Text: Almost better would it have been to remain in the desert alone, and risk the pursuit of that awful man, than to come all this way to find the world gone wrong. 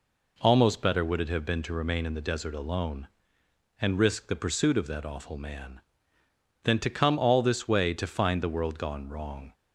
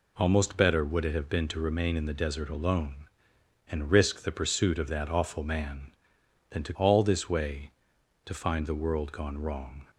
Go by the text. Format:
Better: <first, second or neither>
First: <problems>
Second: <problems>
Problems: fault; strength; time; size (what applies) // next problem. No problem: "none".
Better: first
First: none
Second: skips "come"; at 6.7 s